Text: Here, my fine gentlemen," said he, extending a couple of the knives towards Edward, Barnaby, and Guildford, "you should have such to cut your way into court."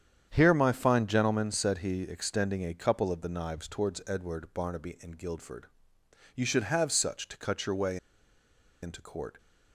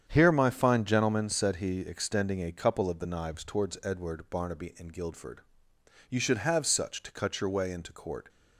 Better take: second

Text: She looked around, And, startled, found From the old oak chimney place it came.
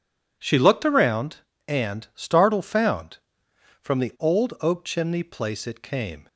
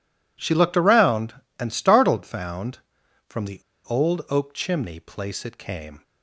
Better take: first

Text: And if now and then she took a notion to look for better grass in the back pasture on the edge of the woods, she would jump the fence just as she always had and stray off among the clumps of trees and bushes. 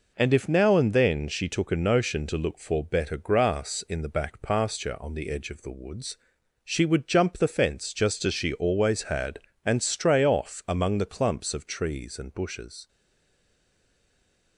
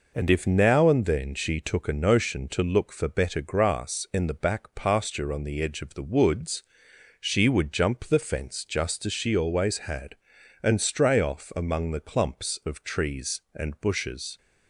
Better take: second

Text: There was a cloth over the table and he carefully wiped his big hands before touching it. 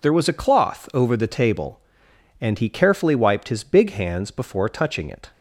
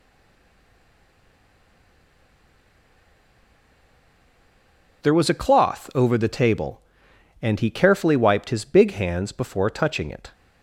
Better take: first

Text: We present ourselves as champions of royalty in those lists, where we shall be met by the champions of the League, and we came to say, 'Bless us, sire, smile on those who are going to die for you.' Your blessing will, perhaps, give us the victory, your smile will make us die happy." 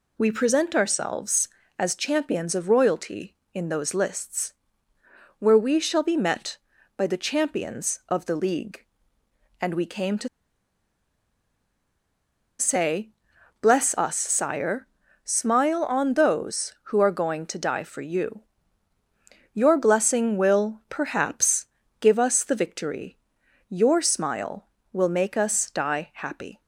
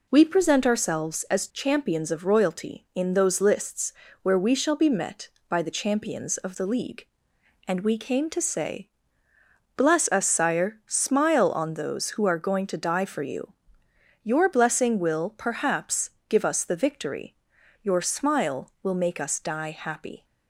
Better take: second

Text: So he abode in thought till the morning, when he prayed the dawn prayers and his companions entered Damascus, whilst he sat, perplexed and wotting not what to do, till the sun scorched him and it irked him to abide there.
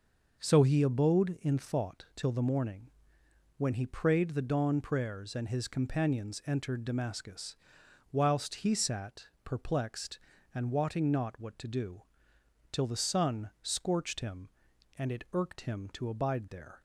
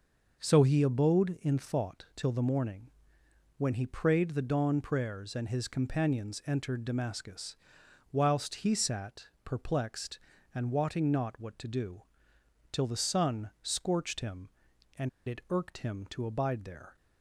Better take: first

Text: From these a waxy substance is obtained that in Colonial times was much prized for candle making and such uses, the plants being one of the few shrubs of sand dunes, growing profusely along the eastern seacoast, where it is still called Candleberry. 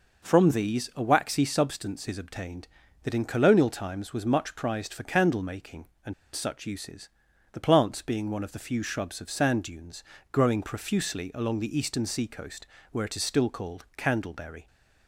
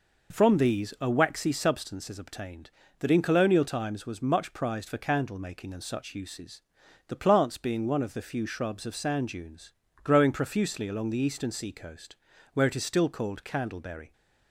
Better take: second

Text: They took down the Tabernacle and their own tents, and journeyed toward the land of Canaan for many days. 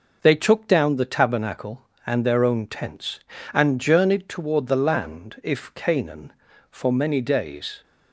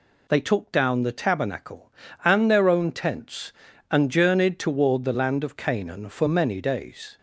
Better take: second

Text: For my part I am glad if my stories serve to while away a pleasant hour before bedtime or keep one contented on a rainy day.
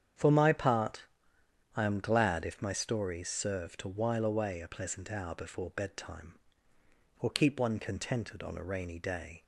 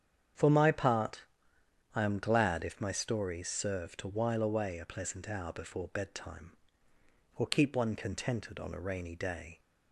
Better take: neither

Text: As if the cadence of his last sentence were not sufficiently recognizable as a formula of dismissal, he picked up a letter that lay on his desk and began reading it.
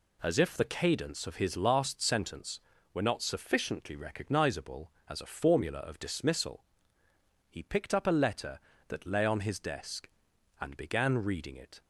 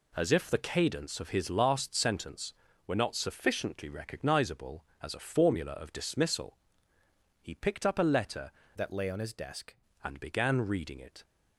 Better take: first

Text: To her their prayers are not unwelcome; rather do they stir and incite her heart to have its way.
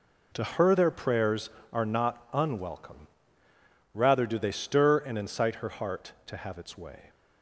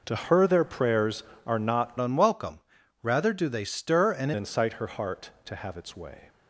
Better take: first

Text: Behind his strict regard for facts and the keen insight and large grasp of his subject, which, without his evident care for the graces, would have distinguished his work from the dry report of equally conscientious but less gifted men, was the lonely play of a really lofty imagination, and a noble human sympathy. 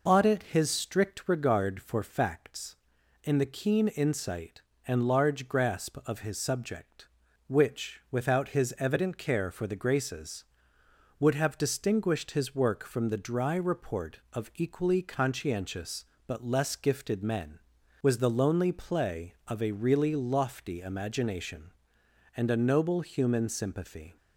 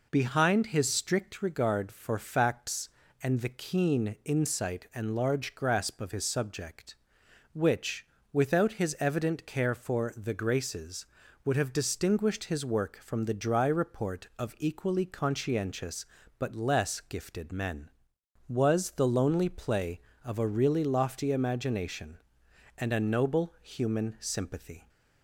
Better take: second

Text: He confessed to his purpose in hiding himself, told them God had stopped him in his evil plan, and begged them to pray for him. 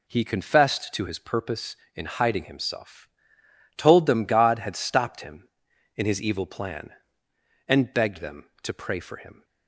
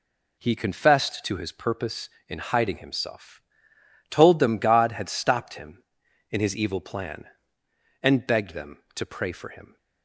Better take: neither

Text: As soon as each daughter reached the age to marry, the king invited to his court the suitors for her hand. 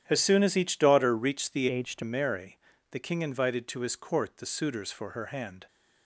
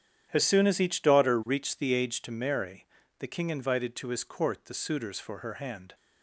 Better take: second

